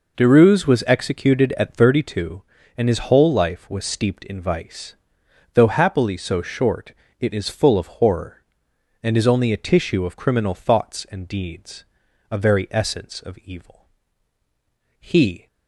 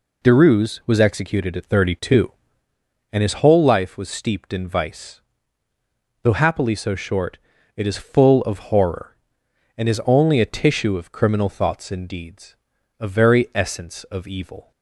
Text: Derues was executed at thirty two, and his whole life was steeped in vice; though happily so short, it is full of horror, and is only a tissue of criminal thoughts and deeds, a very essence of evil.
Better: second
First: goes on to say "He"; slight; from 15.0 s on; 0.46 s long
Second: none

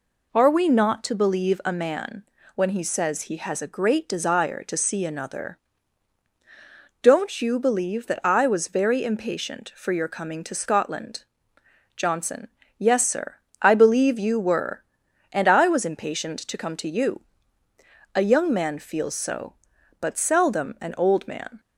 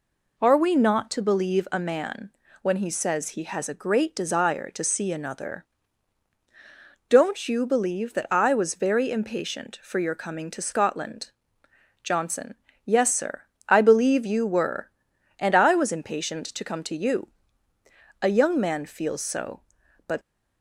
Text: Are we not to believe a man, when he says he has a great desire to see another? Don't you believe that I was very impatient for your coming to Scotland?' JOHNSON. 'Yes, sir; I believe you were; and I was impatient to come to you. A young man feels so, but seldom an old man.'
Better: first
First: none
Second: stops before "seldom an old man"; at 20.2 s

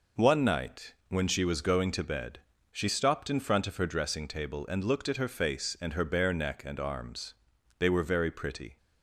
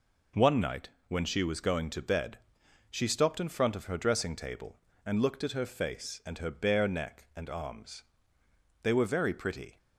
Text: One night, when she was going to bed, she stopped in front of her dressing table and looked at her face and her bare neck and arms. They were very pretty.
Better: neither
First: none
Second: none

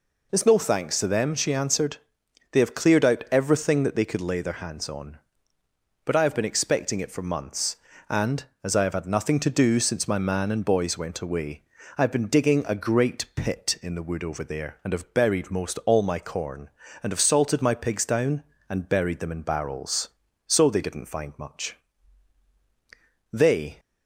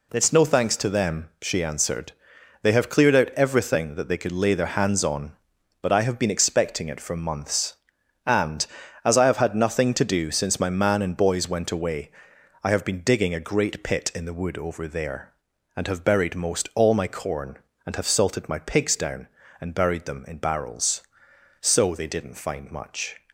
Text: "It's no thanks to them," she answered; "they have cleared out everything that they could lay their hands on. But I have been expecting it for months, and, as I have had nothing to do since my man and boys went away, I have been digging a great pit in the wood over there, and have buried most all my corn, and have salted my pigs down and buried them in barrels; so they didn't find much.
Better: second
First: goes on to say "They"; slight; from 23.3 s on; 0.48 s long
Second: none

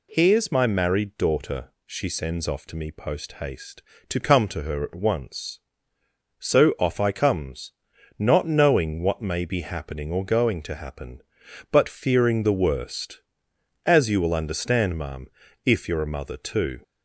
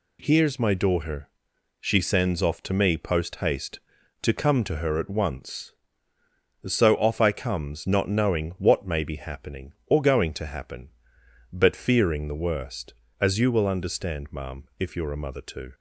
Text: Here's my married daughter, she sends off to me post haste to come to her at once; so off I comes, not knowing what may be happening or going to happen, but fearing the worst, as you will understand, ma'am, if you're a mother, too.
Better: first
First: none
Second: skips "married"; at 0.7 s

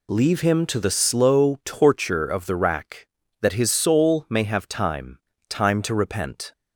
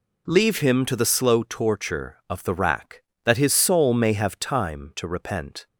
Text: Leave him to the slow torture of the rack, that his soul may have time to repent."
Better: second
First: says "time" twice; at 5.4 s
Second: none

